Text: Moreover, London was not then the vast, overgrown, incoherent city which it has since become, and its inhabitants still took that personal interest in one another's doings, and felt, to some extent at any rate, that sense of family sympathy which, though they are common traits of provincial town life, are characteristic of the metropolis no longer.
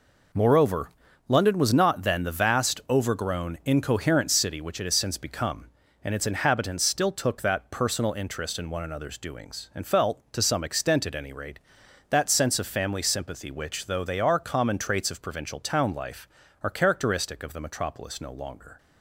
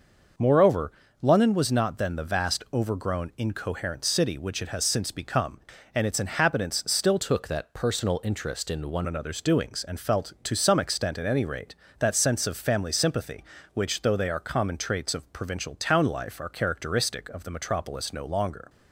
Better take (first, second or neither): first